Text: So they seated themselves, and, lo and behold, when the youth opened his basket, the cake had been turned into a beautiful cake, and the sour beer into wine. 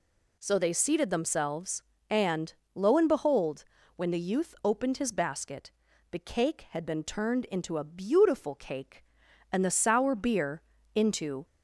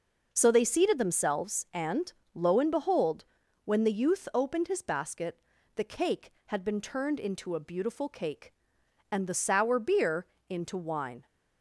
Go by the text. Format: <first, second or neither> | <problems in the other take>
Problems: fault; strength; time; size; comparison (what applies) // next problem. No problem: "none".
second | pauses between "beer" and "into"; slight; at 10.6 s; 0.34 s long; slight in the second // stops before "wine"; at 11.4 s